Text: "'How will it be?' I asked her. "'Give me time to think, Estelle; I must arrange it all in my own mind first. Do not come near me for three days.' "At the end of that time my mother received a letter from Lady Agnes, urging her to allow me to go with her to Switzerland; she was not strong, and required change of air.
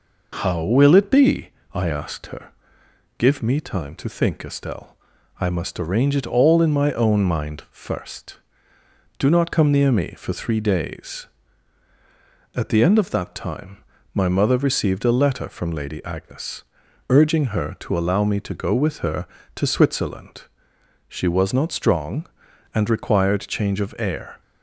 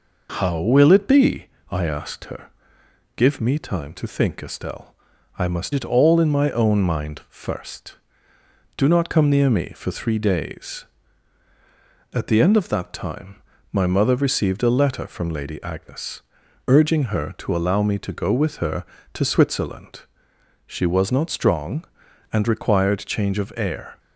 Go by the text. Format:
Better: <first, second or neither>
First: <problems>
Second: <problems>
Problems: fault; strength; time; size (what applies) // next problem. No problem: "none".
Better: first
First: pauses between "time" and "my"; slight; at 13.8 s; 0.30 s long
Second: skips "arrange"; at 5.7 s // pauses between "time" and "my"; slight; at 13.4 s; 0.30 s long